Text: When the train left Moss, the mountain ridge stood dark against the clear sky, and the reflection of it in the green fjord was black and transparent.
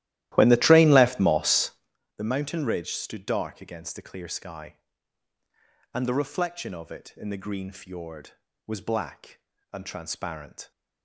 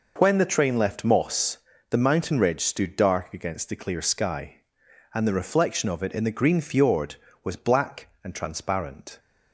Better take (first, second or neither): second